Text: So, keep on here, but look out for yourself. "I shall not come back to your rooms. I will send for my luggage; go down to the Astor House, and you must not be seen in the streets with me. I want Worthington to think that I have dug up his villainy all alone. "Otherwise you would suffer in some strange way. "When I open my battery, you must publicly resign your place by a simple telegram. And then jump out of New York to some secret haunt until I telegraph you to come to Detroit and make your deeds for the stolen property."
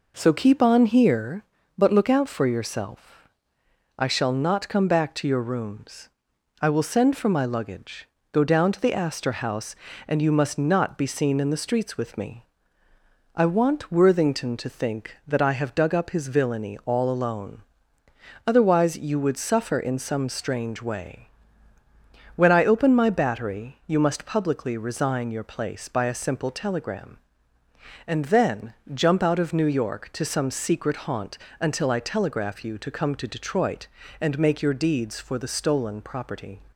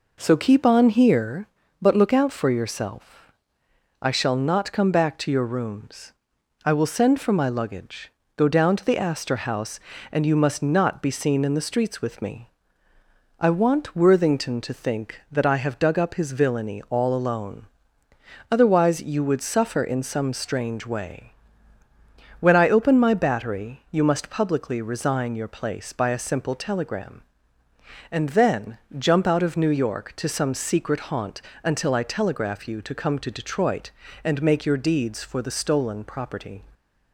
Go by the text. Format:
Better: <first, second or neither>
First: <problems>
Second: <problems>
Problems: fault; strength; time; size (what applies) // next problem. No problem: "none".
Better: neither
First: pauses between "then" and "jump"; slight; at 28.7 s; 0.22 s long // pauses between "haunt" and "until"; slight; at 31.3 s; 0.24 s long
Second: pauses between "then" and "jump"; slight; at 28.7 s; 0.22 s long // pauses between "haunt" and "until"; slight; at 31.4 s; 0.24 s long